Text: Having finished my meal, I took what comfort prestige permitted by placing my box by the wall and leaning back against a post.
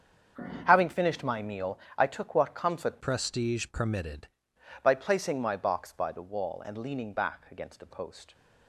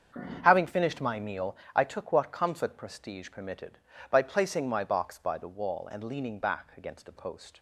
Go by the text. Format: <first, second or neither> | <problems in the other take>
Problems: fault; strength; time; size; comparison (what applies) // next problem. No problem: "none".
second | starts louder than the rest; strong; until 1.6 s; 7 dB; also in the second // changes voice from "prestige" to "permitted"; from 3.0 to 4.2 s; 1.2 s long